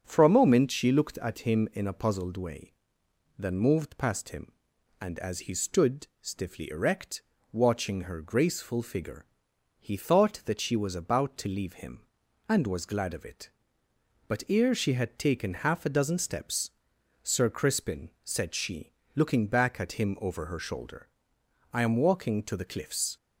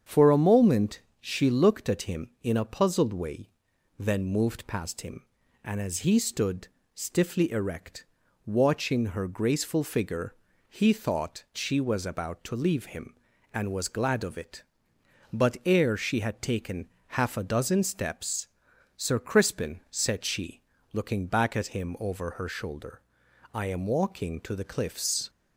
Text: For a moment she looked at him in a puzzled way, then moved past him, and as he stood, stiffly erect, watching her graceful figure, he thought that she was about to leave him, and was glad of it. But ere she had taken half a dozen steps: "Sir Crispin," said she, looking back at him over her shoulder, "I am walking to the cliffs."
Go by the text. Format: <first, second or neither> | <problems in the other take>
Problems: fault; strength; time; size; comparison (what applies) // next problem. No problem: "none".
first | starts louder than the rest; strong; until 1.2 s; 8 dB; also in the first // pauses between "moment" and "she"; slight; at 1.0 s; 0.18 s long // skips "that"; at 11.4 s // pauses between "taken" and "half"; slight; at 16.8 s; 0.28 s long